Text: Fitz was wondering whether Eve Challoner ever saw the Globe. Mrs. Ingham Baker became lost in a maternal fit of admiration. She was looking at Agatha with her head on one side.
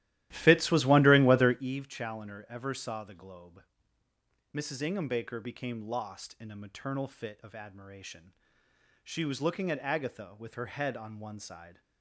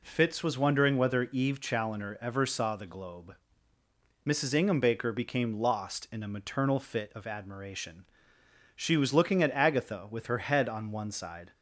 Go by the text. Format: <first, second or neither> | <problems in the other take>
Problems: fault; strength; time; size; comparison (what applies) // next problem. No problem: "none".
second | starts louder than the rest; strong; until 1.7 s; 14.5 dB